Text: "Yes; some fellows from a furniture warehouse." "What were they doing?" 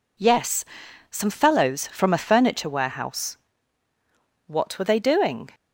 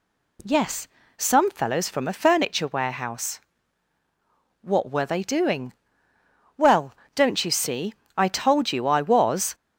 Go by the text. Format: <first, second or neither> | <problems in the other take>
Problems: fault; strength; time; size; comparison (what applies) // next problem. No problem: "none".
first | goes on to say "Well don't you see I told you I was"; strong; from 6.5 s on; 2.9 s long